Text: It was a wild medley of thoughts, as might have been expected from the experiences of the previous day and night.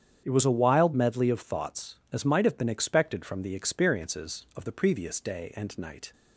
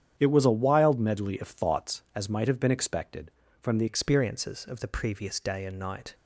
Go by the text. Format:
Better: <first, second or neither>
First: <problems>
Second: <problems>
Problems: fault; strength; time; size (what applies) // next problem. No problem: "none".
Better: first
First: starts louder than the rest; strong; until 1.2 s; 8.5 dB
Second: starts louder than the rest; strong; until 1.1 s; 9 dB // changes voice at "experiences"; from 3.8 s on; 2.3 s long